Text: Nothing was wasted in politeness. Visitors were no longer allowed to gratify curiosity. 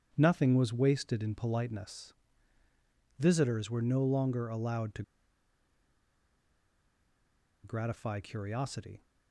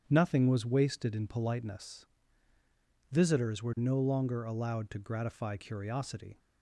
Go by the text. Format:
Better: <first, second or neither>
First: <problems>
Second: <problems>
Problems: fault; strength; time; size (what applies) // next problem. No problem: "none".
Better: second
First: starts louder than the rest; strong; until 1.1 s; 8.5 dB // pauses between "to" and "gratify"; strong; at 5.0 s; 2.6 s long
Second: starts louder than the rest; strong; until 1.0 s; 8.5 dB